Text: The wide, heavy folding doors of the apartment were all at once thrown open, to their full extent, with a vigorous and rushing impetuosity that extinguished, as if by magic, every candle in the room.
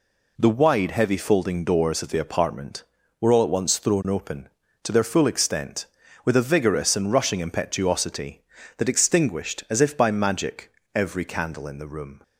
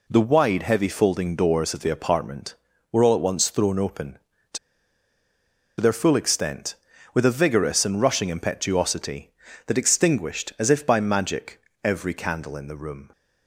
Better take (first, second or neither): first